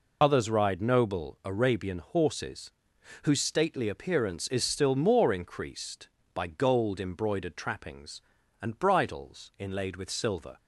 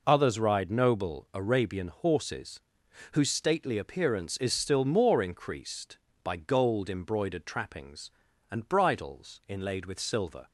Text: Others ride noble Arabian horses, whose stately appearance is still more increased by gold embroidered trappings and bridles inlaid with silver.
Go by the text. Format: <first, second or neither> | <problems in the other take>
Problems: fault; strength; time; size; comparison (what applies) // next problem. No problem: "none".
second | loses the start of "Others"; at 0.2 s; 50 ms